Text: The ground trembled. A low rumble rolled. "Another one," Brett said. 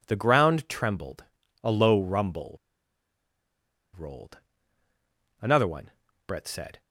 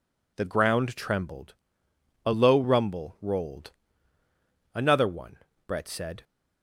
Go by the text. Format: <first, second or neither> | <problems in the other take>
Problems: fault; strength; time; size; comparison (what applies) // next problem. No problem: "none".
second | pauses between "rumble" and "rolled"; strong; at 2.5 s; 1.3 s long